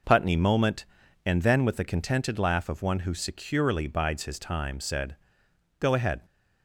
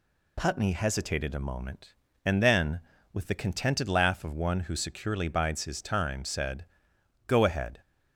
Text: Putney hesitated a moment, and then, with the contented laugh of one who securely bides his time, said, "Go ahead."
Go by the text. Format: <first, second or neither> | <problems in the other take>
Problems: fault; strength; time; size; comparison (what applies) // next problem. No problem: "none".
second | skips "hesitated a"; at 0.3 s